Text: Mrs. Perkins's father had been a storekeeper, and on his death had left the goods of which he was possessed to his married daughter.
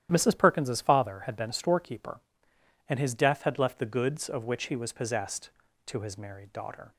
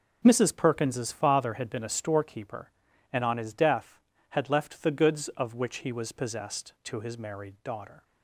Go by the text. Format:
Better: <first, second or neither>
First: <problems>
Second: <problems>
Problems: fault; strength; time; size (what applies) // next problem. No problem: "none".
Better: second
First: starts louder than the rest; strong; until 1.1 s; 11 dB // skips "on"; at 2.9 s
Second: none